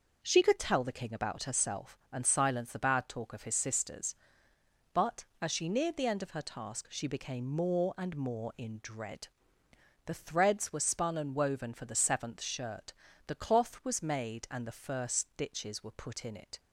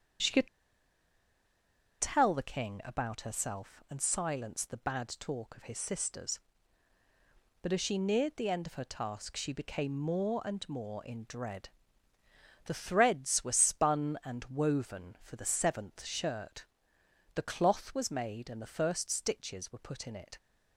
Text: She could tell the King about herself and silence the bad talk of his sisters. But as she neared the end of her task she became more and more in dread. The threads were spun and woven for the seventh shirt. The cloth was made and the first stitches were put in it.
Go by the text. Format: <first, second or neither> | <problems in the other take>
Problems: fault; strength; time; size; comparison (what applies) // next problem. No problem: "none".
first | starts louder than the rest; strong; until 2.7 s; 7 dB // pauses between "could" and "tell"; strong; at 0.4 s; 1.5 s long